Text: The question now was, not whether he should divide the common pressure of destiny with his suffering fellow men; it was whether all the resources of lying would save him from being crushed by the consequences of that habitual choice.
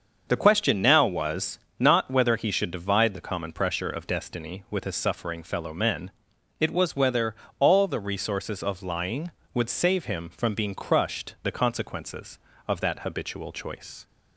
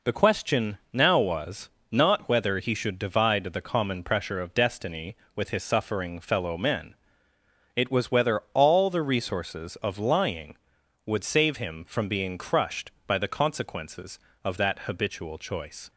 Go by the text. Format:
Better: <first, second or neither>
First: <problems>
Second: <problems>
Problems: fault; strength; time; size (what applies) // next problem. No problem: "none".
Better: second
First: starts louder than the rest; until 1.2 s; 6.5 dB // pauses between "whether" and "all"; slight; at 7.3 s; 0.28 s long // skips "by"; at 11.3 s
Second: none